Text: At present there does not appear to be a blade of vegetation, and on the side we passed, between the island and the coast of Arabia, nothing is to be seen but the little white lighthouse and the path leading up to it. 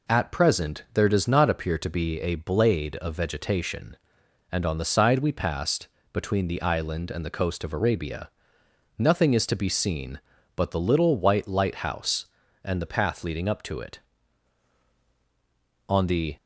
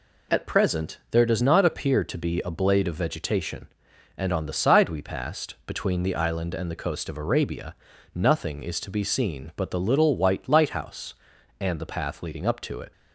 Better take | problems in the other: second | goes on to say "On the"; slight; from 15.8 s on; 0.48 s long

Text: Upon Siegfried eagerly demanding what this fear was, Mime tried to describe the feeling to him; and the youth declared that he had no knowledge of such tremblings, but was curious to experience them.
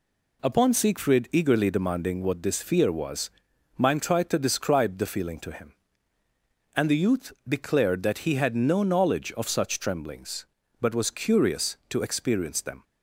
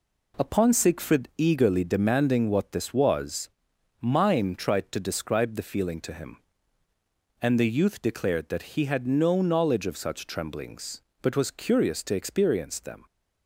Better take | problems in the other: first | skips "fear"; at 2.9 s

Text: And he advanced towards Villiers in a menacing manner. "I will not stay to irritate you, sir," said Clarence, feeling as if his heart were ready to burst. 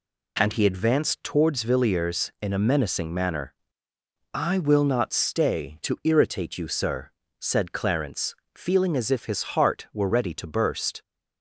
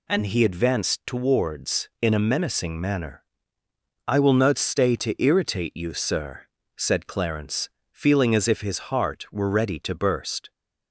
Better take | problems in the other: first | skips "Villiers"; at 1.9 s

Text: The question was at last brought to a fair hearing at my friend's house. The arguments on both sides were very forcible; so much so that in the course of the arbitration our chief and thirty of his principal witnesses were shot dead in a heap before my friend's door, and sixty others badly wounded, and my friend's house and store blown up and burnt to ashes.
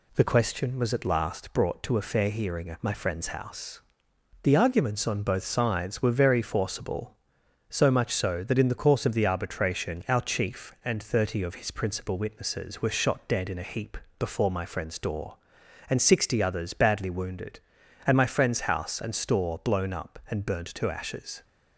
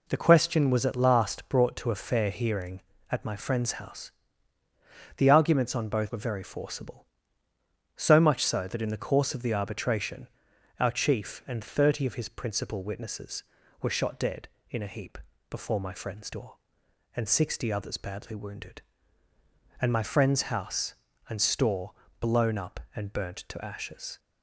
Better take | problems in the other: first | skips "sides"; at 6.1 s // pauses between "arbitration" and "our"; noticeable; at 10.2 s; 0.50 s long // pauses between "heap" and "before"; slight; at 15.1 s; 0.32 s long; slight in the first // pauses between "store" and "blown"; slight; at 21.9 s; 0.28 s long

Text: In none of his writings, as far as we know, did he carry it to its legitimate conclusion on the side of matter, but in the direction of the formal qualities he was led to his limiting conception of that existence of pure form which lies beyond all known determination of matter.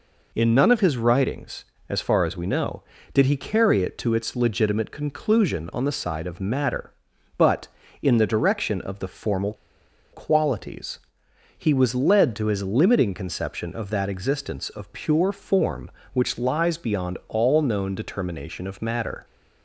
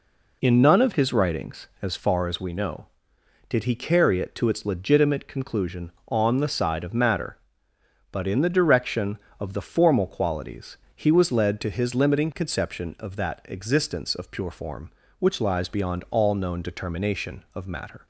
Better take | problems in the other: second | pauses between "formal" and "qualities"; noticeable; at 9.5 s; 0.58 s long // pauses between "qualities" and "he"; noticeable; at 10.9 s; 0.58 s long; slight in the second

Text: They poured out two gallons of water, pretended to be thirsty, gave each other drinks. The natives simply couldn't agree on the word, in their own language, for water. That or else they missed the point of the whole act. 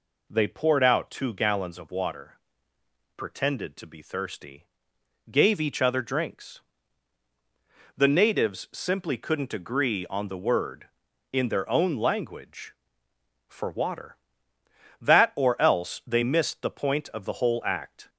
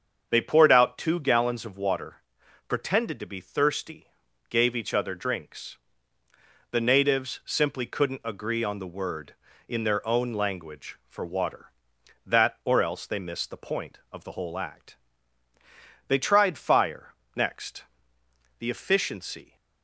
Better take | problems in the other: first | starts louder than the rest; until 1.3 s; 7 dB // goes on to say "They tried fire next The efficiency"; strong; from 16.0 s on; 3.4 s long

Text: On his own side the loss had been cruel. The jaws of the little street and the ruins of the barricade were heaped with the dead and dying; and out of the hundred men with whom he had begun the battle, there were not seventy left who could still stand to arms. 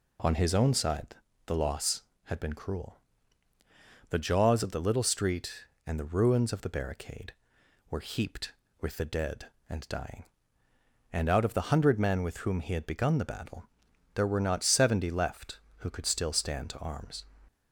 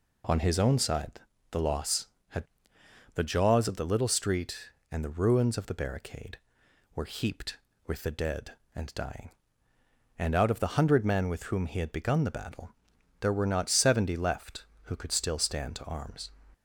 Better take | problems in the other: first | pauses between "side" and "the"; slight; at 1.1 s; 0.32 s long; slight in the first // skips "been cruel"; at 2.7 s

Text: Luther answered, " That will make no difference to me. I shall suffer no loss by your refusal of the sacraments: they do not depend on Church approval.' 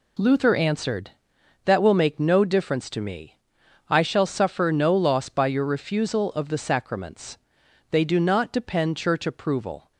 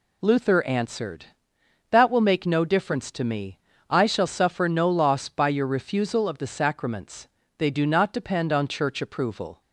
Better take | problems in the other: second | skips "on"; at 8.9 s

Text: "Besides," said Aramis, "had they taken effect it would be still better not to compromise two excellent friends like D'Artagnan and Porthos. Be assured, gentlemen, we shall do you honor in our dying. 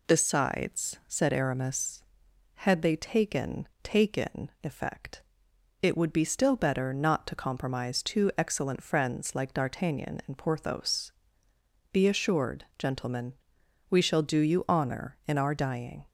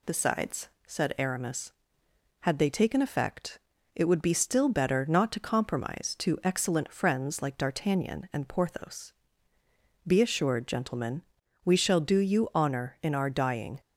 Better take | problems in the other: second | says "taken" twice; at 3.8 s // pauses between "effect" and "it"; noticeable; at 5.2 s; 0.58 s long; slight in the second

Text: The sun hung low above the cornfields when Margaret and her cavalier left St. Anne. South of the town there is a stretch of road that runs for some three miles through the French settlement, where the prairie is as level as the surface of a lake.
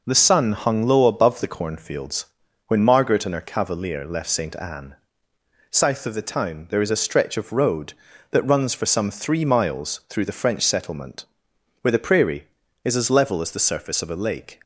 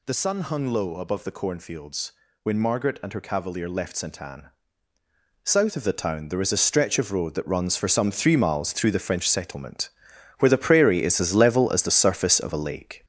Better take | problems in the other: first | gets louder; noticeable; throughout; 6 dB // pauses between "cornfields" and "when"; slight; at 2.1 s; 0.32 s long; also in the first

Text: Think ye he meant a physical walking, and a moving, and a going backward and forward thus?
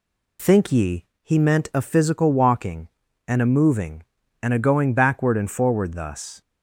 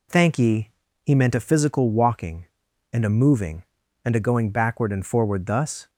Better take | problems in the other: first | says "Thank" for "Think"; at 0.0 s // pauses between "ye" and "he"; slight; at 0.7 s; 0.32 s long; slight in the first

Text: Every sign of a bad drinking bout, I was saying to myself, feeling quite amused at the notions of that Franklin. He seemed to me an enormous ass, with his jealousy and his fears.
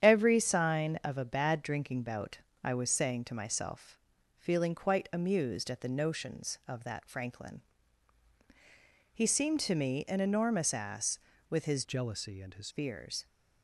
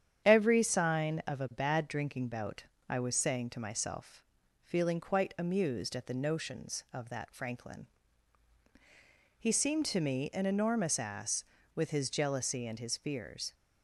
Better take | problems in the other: second | starts louder than the rest; strong; until 1.0 s; 9 dB; strong in the second // changes voice from "jealousy" to "his"; from 11.8 to 12.6 s; 0.8 s long

